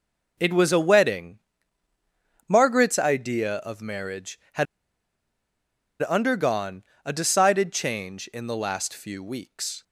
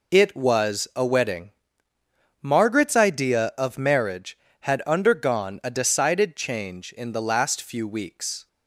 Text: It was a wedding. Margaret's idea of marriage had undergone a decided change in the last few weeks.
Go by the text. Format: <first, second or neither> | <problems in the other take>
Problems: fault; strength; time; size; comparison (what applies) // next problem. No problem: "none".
second | pauses between "had" and "undergone"; strong; at 4.6 s; 1.3 s long // pauses between "undergone" and "a"; slight; at 6.8 s; 0.20 s long